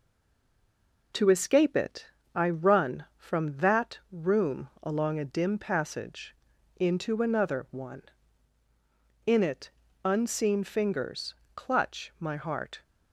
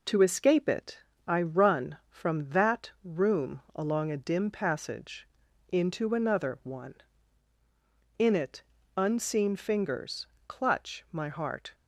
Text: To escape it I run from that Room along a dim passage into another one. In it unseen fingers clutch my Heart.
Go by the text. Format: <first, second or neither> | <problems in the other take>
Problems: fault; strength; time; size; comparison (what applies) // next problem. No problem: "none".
second | stays silent before the first word; until 1.1 s; 1.1 s long // pauses between "it" and "I"; slight; at 2.0 s; 0.30 s long; slight in the second // pauses between "passage" and "into"; at 6.3 s; 0.40 s long; also in the second // pauses between "it" and "unseen"; slight; at 9.7 s; 0.34 s long; slight in the second // pauses between "fingers" and "clutch"; slight; at 11.3 s; 0.22 s long; slight in the second